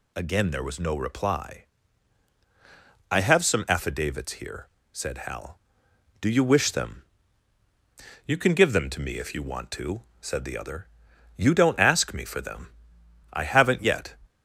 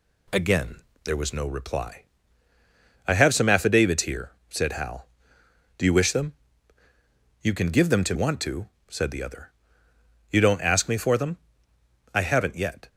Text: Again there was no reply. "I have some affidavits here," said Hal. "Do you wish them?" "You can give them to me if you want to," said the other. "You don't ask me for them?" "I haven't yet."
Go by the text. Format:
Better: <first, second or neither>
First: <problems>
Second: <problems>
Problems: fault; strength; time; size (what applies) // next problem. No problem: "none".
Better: first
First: none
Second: pauses between "Again" and "there"; slight; at 0.8 s; 0.24 s long // skips "me if you"; at 8.1 s